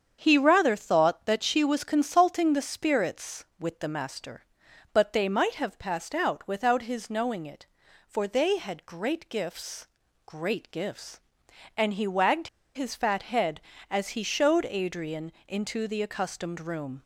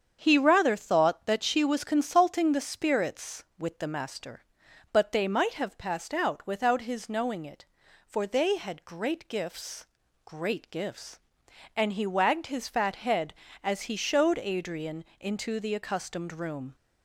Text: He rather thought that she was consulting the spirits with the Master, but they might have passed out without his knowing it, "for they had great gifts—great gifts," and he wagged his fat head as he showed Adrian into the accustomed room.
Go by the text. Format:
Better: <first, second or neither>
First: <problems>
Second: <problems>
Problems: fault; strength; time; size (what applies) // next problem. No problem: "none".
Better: second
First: starts louder than the rest; strong; until 1.2 s; 7.5 dB // pauses between "wagged" and "his"; slight; at 12.4 s; 0.26 s long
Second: starts louder than the rest; strong; until 1.2 s; 7.5 dB